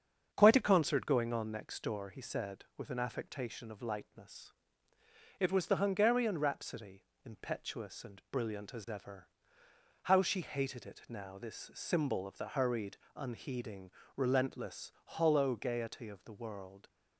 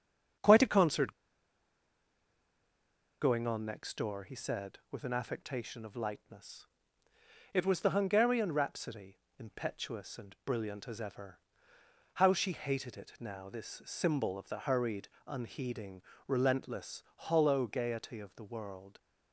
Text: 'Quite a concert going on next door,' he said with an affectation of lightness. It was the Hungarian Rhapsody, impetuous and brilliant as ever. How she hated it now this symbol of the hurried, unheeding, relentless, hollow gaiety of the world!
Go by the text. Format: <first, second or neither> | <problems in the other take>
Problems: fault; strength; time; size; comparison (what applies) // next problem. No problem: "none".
first | starts louder than the rest; strong; until 3.5 s; 7.5 dB; strong in the first // pauses between "concert" and "going"; strong; at 1.1 s; 2.0 s long